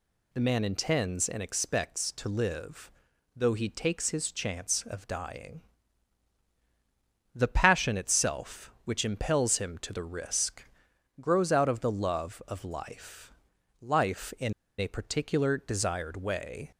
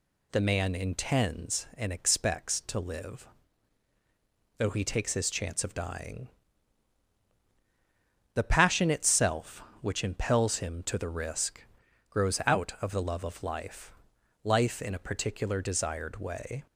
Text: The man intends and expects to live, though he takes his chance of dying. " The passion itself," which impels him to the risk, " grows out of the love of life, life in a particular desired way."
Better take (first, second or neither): second